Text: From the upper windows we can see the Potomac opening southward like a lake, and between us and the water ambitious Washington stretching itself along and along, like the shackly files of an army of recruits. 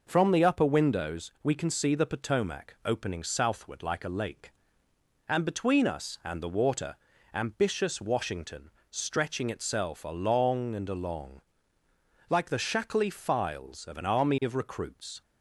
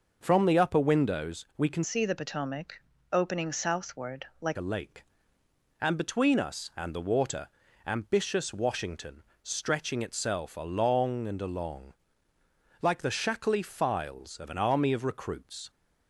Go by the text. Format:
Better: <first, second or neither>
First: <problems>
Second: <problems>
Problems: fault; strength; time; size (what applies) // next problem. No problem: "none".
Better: first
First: pauses between "water" and "ambitious"; at 6.9 s; 0.38 s long // pauses between "Washington" and "stretching"; slight; at 8.6 s; 0.20 s long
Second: changes voice from "see" to "like"; from 1.8 to 4.5 s; 2.7 s long // pauses between "Potomac" and "opening"; slight; at 2.8 s; 0.32 s long // pauses between "water" and "ambitious"; at 7.4 s; 0.38 s long // pauses between "Washington" and "stretching"; slight; at 9.2 s; 0.20 s long